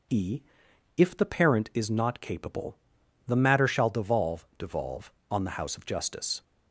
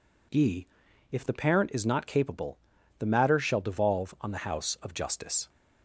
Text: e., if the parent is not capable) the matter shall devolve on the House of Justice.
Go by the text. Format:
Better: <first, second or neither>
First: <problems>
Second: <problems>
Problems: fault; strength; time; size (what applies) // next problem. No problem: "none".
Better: second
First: says "devolve" twice; at 4.5 s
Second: none